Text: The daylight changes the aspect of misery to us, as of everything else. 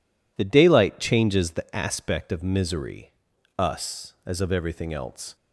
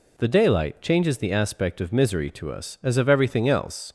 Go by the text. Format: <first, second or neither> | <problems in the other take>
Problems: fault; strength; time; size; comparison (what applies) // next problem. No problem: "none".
second | skips "to"; at 3.3 s